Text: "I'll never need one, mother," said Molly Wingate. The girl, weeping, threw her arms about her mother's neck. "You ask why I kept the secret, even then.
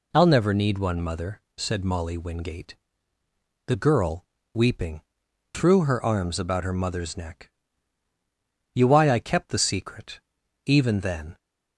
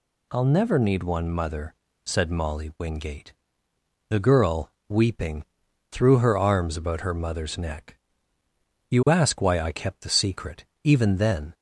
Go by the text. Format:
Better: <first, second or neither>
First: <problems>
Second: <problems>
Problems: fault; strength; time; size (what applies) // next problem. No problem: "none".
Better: second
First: skips "ask"; at 8.8 s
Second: none